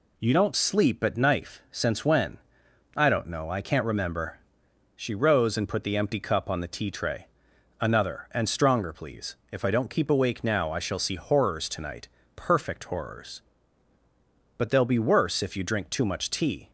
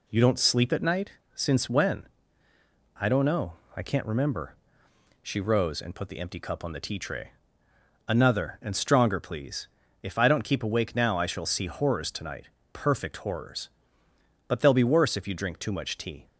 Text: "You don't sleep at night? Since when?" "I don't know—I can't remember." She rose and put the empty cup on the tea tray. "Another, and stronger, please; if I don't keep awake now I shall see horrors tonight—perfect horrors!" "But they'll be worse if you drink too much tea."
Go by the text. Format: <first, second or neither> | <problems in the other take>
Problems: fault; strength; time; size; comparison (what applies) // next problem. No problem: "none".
second | says "knife" for "night"; at 1.1 s